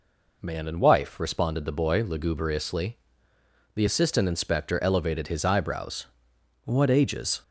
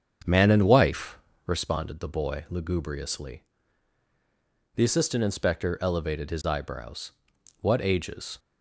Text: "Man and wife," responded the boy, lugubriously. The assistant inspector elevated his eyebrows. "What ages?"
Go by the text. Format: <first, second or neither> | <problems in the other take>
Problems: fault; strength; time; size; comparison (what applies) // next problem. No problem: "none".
first | starts louder than the rest; strong; until 1.7 s; 7 dB